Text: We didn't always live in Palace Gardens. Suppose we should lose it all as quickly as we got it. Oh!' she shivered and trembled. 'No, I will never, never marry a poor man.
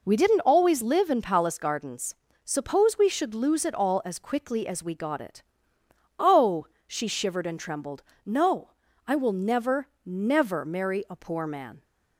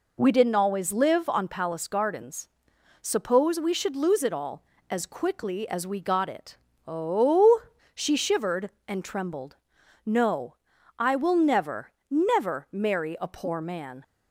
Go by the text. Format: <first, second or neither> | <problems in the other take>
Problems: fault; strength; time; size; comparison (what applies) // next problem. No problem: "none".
first | says "on" for "in"; at 1.2 s